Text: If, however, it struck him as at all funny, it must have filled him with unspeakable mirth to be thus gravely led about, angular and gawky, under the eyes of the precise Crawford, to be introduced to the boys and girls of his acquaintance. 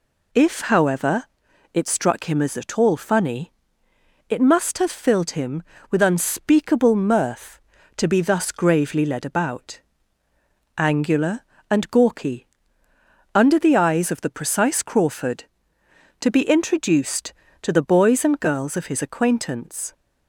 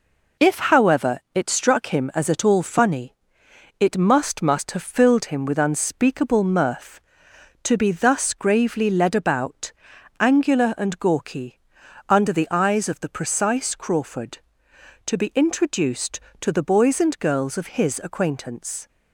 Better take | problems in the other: first | says "must" twice; at 4.4 s

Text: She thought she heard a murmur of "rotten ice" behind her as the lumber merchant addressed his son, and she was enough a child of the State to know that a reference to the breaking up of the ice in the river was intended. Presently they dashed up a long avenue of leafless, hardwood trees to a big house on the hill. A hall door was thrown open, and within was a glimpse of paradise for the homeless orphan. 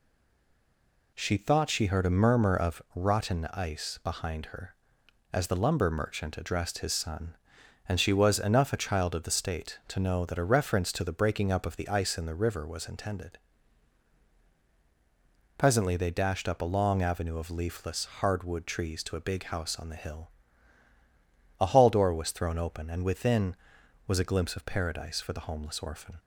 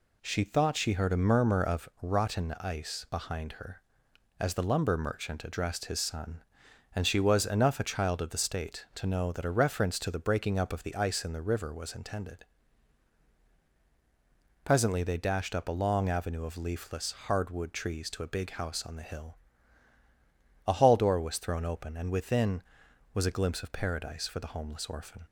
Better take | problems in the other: second | stays silent before the first word; until 1.1 s; 1.1 s long

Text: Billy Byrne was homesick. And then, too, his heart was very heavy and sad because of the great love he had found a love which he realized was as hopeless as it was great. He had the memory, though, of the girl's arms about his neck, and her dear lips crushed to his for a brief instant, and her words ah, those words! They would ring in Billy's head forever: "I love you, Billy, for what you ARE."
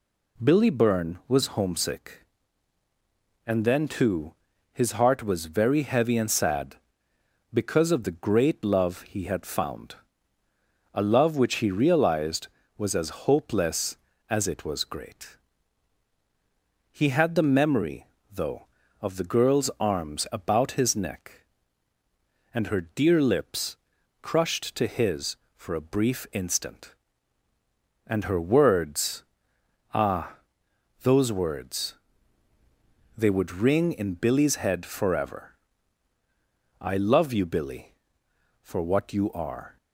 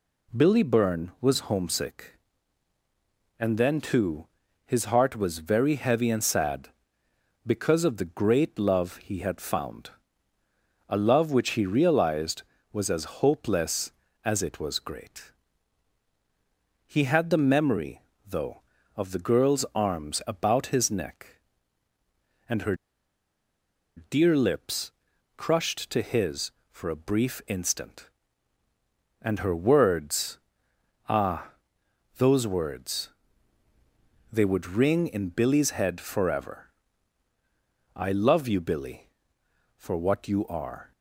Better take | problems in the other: first | pauses between "found" and "a"; at 9.8 s; 1.0 s long; also in the first // pauses between "her" and "dear"; at 22.7 s; 1.2 s long // pauses between "lips" and "crushed"; noticeable; at 24.8 s; 0.46 s long; noticeable in the first // pauses between "words" and "ah"; noticeable; at 30.3 s; 0.70 s long; noticeable in the first

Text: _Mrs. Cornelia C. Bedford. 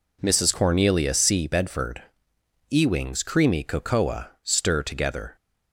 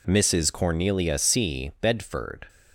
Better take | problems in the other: second | goes on to say "EWING'S CREAMY COCOA Stir together"; strong; from 2.6 s on; 2.6 s long

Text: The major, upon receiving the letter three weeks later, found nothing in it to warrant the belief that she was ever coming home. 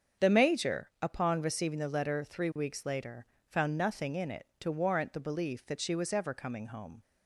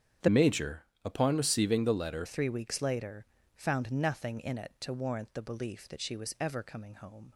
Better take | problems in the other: first | starts louder than the rest; strong; until 1.4 s; 9 dB; strong in the first // changes voice from "major" to "letter"; from 0.2 to 2.2 s; 2.0 s long

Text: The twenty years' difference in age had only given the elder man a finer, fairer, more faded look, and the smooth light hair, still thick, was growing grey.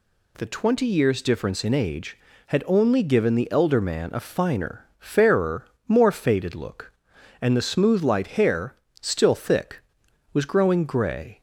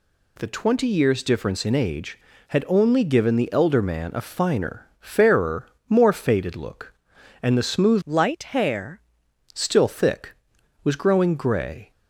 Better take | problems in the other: first | changes voice from "light" to "hair"; from 8.0 to 8.9 s; 0.9 s long

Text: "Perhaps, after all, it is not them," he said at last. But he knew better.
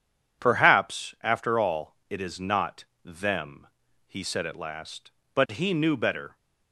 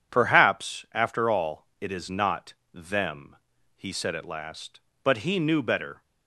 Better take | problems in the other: neither | pauses between "not" and "them"; slight; the same in both

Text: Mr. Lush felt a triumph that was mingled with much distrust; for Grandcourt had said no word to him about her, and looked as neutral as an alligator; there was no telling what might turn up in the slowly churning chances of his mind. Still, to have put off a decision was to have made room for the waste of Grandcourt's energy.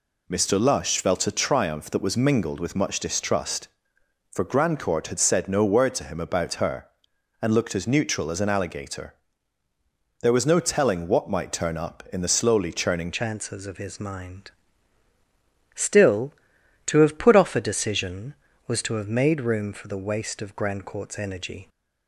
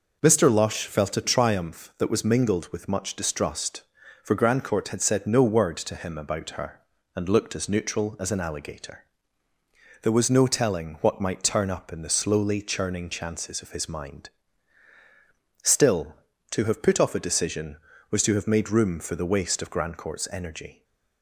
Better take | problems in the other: second | changes voice at "chances"; from 13.1 s on; 8.5 s long

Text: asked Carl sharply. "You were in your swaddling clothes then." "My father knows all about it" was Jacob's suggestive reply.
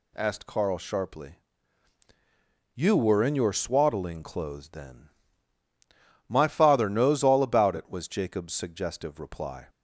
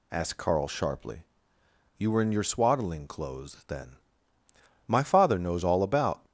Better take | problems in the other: first | stops before "it was Jacob's suggestive reply"; at 6.2 s

